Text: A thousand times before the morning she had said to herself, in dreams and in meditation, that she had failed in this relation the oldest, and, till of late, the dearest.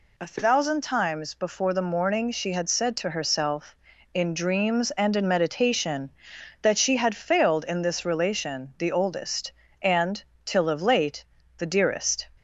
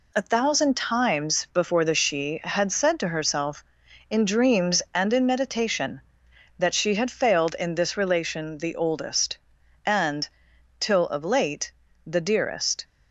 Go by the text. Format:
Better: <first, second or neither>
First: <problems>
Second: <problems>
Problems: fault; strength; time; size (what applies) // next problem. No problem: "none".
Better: first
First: none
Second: skips "morning"; at 1.9 s